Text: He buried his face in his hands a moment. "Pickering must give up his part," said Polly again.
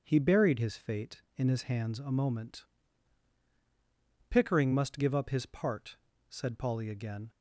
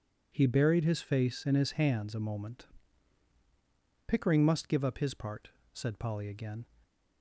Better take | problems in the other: second | starts louder than the rest; until 1.0 s; 6.5 dB // says "fate" for "face"; at 0.7 s

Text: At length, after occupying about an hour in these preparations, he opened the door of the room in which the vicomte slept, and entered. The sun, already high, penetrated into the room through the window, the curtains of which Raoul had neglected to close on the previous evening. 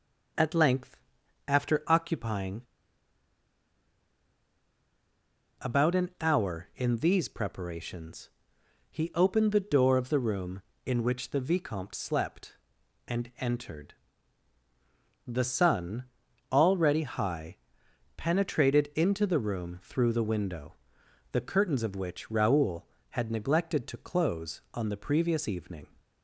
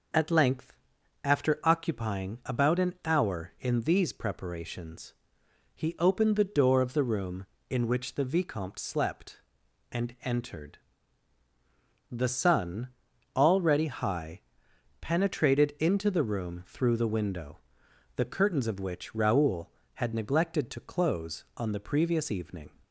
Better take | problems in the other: second | pauses between "occupying" and "about"; strong; at 2.6 s; 2.9 s long

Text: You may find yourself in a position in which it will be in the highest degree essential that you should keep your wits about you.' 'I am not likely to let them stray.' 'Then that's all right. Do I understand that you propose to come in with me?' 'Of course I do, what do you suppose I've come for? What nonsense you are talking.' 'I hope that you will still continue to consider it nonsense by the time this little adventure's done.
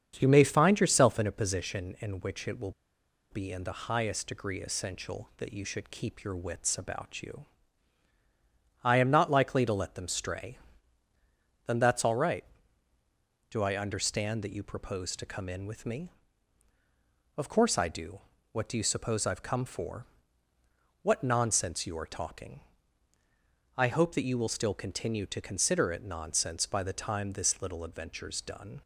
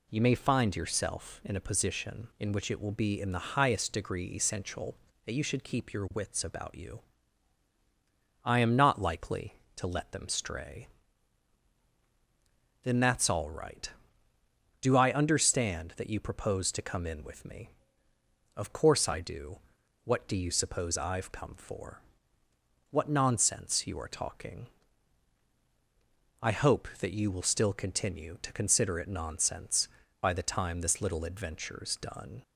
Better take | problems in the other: second | starts louder than the rest; strong; until 1.2 s; 7.5 dB // pauses between "will" and "be"; noticeable; at 2.7 s; 0.60 s long

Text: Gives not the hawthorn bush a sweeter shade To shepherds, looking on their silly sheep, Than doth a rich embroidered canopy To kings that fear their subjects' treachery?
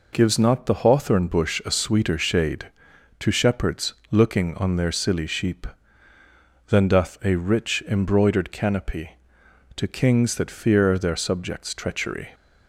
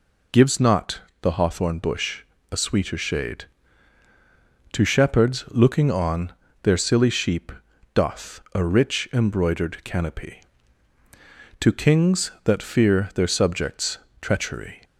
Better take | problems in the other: first | pauses between "not" and "the"; slight; at 0.9 s; 0.22 s long // pauses between "bush" and "a"; slight; at 2.2 s; 0.30 s long // pauses between "on" and "their"; slight; at 6.3 s; 0.30 s long // skips "Than"; at 7.7 s // pauses between "subjects" and "treachery"; slight; at 13.9 s; 0.24 s long

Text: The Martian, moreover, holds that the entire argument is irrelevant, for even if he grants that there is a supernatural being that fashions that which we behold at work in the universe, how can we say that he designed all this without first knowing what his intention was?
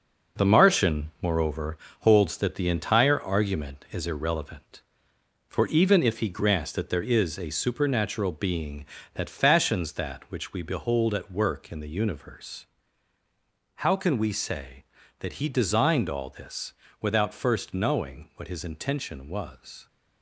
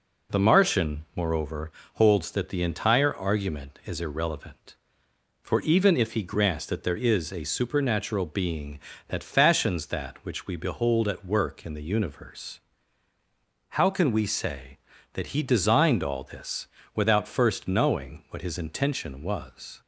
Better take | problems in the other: second | gets quieter; throughout; 6.5 dB // pauses between "this" and "without"; slight; at 16.7 s; 0.26 s long; slight in the second

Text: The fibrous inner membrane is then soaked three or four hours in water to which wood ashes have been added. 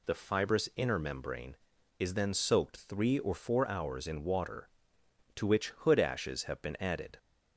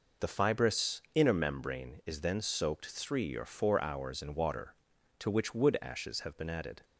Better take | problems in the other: second | says "hood" for "wood"; at 5.6 s

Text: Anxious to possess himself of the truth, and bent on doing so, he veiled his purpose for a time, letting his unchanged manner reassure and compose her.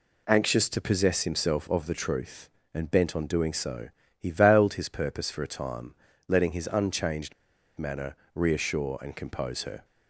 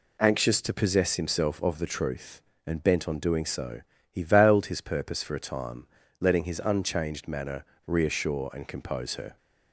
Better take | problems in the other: second | pauses between "unchanged" and "manner"; at 7.3 s; 0.44 s long // pauses between "manner" and "reassure"; slight; at 8.1 s; 0.18 s long; slight in the second

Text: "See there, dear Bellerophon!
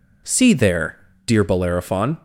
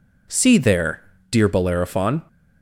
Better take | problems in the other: neither | none

